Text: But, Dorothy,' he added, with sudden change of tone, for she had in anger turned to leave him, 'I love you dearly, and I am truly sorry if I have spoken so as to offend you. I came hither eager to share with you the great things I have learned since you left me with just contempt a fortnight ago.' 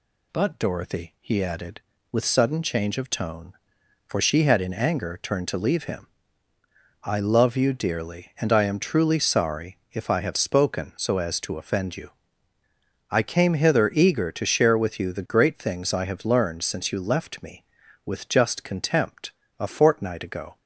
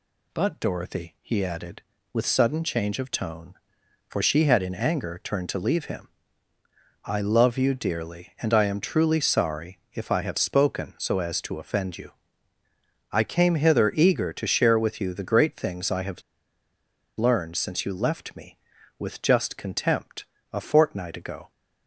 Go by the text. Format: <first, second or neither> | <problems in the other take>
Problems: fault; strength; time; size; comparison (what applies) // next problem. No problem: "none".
first | pauses between "have" and "learned"; noticeable; at 16.2 s; 0.95 s long // pauses between "contempt" and "a"; slight; at 20.2 s; 0.26 s long; slight in the first